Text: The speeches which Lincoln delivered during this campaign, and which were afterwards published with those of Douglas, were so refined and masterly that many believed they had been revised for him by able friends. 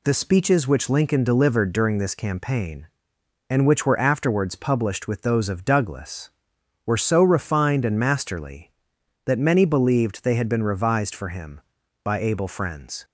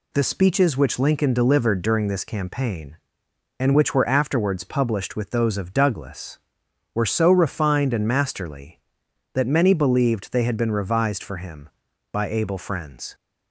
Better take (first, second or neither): neither